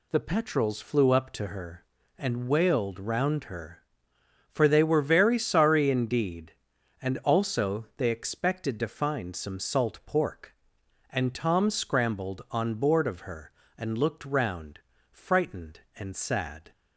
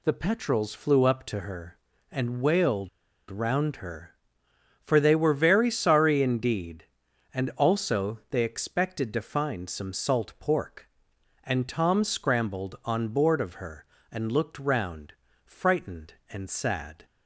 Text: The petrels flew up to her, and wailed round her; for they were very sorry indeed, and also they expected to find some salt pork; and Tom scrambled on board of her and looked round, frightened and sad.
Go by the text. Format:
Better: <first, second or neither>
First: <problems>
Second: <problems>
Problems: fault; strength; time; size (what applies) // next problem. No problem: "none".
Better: first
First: none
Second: pauses between "wailed" and "round"; at 2.8 s; 0.41 s long